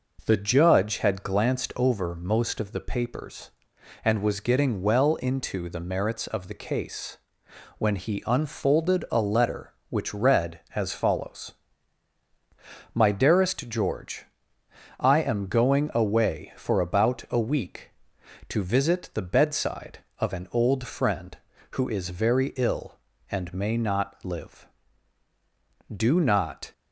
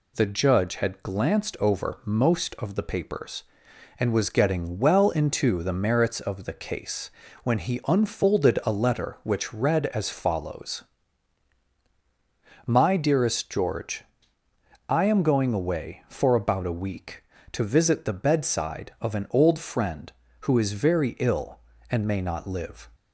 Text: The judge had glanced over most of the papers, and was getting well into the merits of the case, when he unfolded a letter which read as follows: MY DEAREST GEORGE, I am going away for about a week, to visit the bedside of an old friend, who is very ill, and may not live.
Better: second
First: goes on to say "Do not"; noticeable; from 25.9 s on; 0.76 s long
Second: none

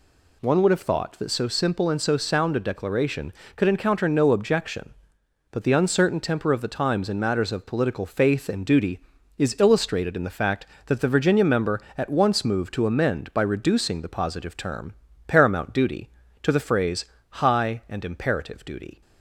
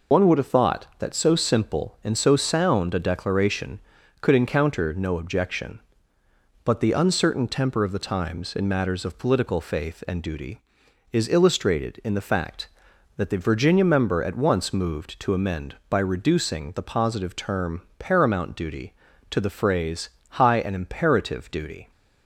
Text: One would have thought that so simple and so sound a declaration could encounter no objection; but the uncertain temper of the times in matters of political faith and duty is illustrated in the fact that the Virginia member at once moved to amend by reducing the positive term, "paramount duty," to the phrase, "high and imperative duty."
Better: first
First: none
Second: loses the start of "One"; at 0.1 s; 65 ms

